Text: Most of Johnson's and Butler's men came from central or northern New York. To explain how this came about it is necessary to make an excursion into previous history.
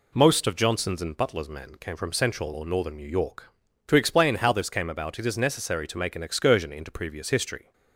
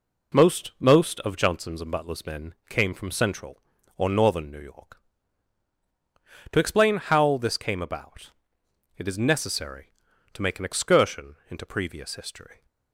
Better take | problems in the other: first | says "Most" twice; at 0.7 s // pauses between "about" and "it"; noticeable; at 8.3 s; 0.66 s long

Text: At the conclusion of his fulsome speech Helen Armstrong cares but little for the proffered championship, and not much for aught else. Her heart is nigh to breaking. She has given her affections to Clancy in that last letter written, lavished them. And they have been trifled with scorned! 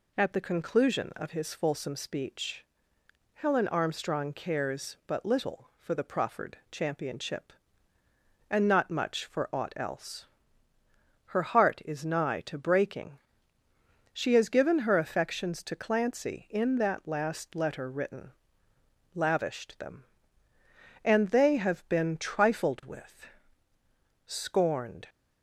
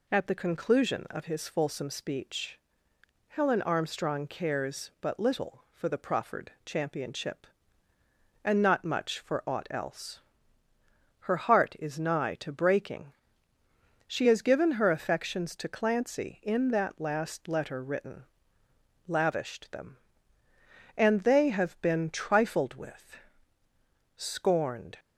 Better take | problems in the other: neither | pauses between "speech" and "Helen"; noticeable; the same in both // pauses between "with" and "scorned"; noticeable; the same in both

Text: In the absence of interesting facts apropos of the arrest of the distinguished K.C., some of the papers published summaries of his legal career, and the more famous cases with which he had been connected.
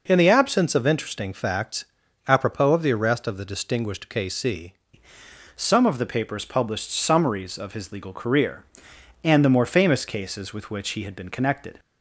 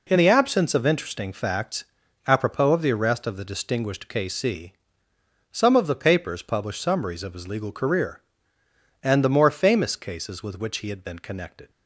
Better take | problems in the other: second | pauses between "facts" and "apropos"; at 1.8 s; 0.44 s long; also in the second // changes voice at "some"; from 5.5 s on; 6.2 s long

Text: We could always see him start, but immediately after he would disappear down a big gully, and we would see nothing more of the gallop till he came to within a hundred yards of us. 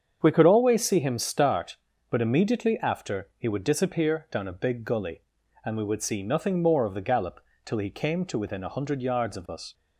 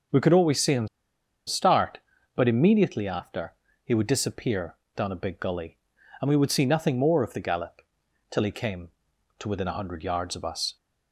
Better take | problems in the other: first | starts louder than the rest; until 1.7 s; 6 dB; strong in the first // pauses between "him" and "start"; noticeable; at 0.8 s; 0.59 s long // pauses between "after" and "he"; slight; at 3.5 s; 0.30 s long // pauses between "disappear" and "down"; slight; at 4.7 s; 0.20 s long // pauses between "gallop" and "till"; noticeable; at 7.8 s; 0.48 s long; slight in the first

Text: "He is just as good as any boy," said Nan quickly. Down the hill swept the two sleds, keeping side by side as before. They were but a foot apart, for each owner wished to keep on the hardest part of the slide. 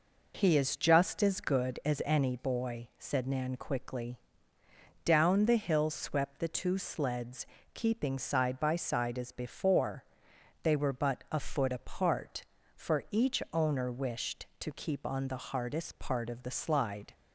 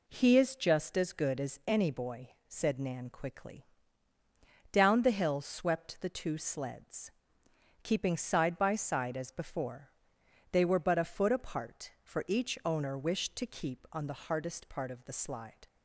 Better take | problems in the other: neither | none

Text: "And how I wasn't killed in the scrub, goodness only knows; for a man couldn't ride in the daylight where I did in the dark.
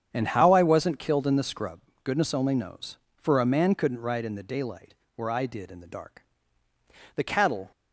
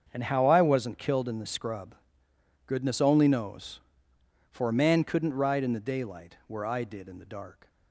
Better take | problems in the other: second | starts louder than the rest; strong; until 1.1 s; 8 dB; also in the second // pauses between "daylight" and "where"; slight; at 4.9 s; 0.22 s long // goes on to say "The cattle"; from 7.1 s on; 0.56 s long

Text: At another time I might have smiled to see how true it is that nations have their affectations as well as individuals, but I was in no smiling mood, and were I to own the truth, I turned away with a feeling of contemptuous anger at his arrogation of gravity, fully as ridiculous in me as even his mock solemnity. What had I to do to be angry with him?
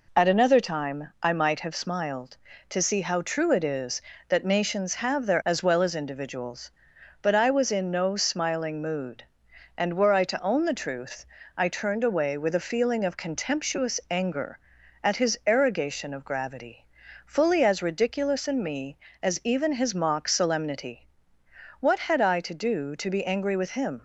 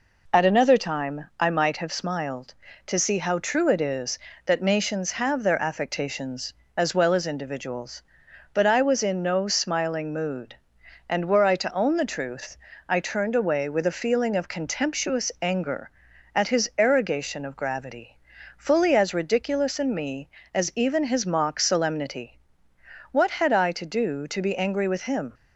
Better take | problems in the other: second | skips "affectations"; at 5.4 s

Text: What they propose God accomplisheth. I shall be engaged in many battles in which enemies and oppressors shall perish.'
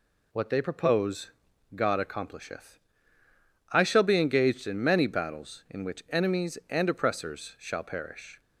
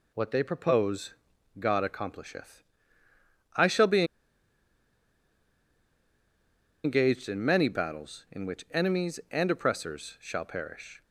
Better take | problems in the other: first | pauses between "propose" and "God"; at 1.1 s; 0.44 s long; also in the first // pauses between "be" and "engaged"; strong; at 4.0 s; 2.8 s long

